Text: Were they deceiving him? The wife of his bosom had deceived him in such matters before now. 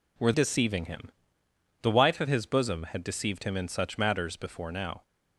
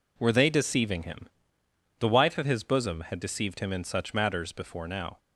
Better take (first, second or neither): second